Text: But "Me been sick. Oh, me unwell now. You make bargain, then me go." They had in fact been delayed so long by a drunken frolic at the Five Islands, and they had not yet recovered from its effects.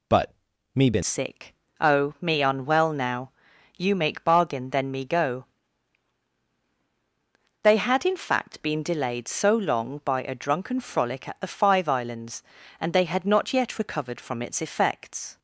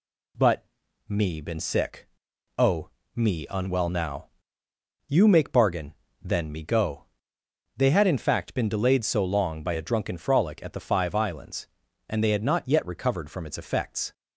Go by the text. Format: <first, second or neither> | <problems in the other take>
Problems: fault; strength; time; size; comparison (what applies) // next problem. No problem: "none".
second | pauses between "But" and "Me"; at 0.3 s; 0.40 s long; also in the second // changes voice at "sick"; from 1.0 s on; 14.3 s long